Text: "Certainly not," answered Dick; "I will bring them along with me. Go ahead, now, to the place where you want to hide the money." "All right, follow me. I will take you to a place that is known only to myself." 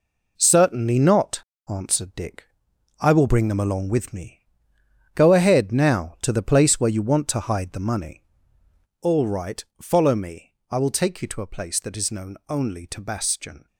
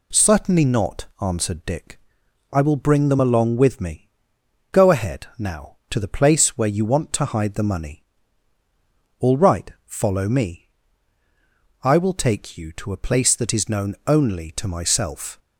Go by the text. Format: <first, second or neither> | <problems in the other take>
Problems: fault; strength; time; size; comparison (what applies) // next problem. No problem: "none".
second | says "bastion" for "myself"; at 13.0 s